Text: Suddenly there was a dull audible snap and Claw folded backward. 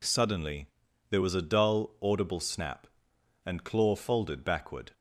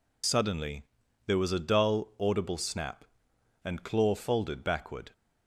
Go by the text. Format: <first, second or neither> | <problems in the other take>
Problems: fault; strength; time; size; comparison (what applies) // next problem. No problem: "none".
first | loses the start of "Suddenly"; at 0.2 s; 55 ms // pauses between "Suddenly" and "there"; at 0.8 s; 0.44 s long; also in the first